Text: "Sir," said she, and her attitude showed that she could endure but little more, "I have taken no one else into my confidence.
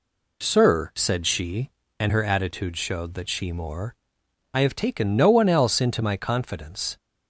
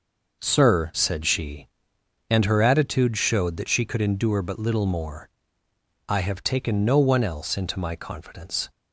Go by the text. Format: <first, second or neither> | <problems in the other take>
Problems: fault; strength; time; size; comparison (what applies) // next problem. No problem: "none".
second | skips "could endure but little"; at 3.5 s